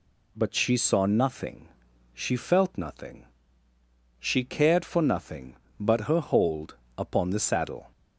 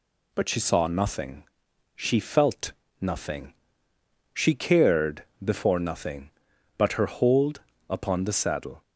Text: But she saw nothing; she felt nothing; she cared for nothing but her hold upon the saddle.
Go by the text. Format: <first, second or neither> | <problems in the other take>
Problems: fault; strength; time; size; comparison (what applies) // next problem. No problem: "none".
first | pauses between "felt" and "nothing"; slight; at 2.7 s; 0.30 s long // says "before" for "for"; at 5.4 s // pauses between "hold" and "upon"; slight; at 7.5 s; 0.30 s long; slight in the first